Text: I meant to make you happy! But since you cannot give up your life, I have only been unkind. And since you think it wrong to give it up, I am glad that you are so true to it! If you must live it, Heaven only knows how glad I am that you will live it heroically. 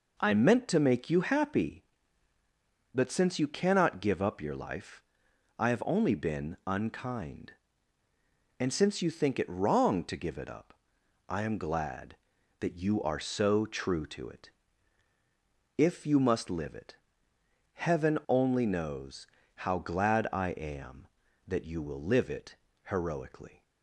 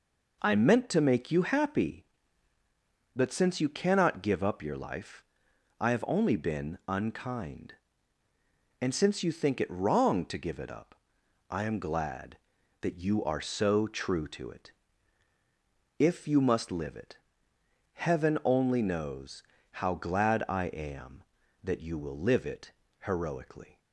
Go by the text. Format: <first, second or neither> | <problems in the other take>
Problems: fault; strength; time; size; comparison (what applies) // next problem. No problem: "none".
neither | pauses between "knows" and "how"; slight; the same in both // pauses between "it" and "heroically"; slight; the same in both